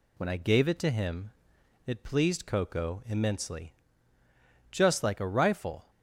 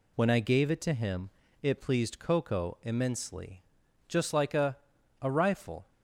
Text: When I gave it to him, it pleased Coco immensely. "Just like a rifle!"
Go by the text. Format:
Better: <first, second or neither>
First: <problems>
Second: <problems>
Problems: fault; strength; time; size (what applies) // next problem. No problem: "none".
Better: first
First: none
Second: says "a" twice; at 5.2 s